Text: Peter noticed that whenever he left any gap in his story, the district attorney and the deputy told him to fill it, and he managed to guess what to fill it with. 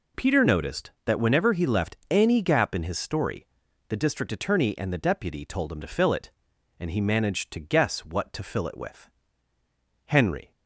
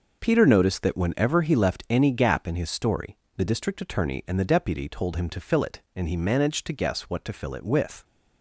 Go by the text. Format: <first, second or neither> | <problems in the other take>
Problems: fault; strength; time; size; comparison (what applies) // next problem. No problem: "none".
second | goes on to say "Henry"; slight; from 10.0 s on; 0.46 s long